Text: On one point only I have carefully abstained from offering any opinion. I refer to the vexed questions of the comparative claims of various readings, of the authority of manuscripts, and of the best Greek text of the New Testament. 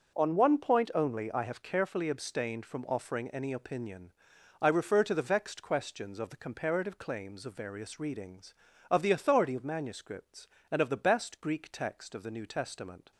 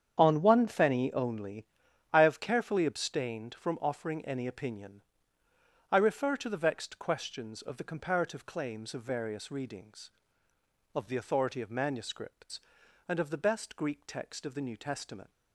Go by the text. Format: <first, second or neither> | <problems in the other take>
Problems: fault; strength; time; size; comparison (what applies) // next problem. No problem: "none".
first | starts louder than the rest; strong; until 1.1 s; 8.5 dB // says "fenny" for "point"; at 0.6 s // pauses between "only" and "I"; noticeable; at 1.6 s; 0.48 s long